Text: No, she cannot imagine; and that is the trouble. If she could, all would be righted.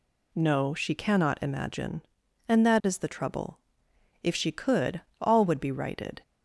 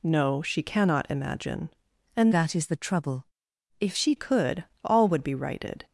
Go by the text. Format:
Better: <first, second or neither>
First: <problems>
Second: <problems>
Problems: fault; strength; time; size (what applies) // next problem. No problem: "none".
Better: first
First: none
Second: changes voice from "that" to "she"; from 2.3 to 4.1 s; 1.8 s long